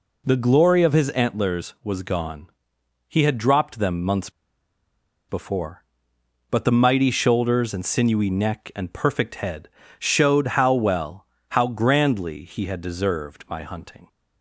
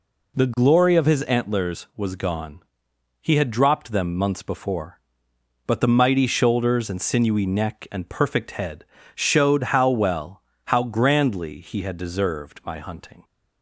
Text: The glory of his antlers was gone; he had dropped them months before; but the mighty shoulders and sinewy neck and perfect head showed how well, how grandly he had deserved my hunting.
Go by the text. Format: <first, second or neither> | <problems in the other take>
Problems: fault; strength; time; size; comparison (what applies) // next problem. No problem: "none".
second | pauses between "months" and "before"; noticeable; at 4.3 s; 0.97 s long // pauses between "head" and "showed"; slight; at 9.6 s; 0.32 s long; slight in the second